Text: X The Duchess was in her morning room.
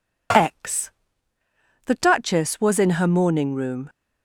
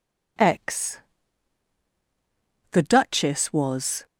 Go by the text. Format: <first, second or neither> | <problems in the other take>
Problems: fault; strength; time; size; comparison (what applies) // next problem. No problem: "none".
first | pauses between "X" and "The"; strong; at 0.9 s; 1.7 s long; noticeable in the first // stops before "in her morning room"; at 4.0 s